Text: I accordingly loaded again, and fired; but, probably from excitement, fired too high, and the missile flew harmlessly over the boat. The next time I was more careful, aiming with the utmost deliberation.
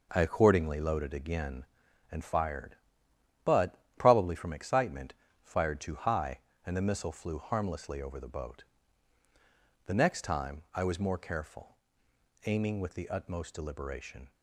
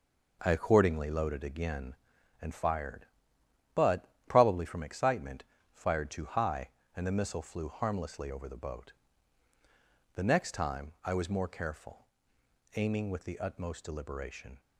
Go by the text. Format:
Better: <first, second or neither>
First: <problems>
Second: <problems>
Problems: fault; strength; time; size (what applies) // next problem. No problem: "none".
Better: neither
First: none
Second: none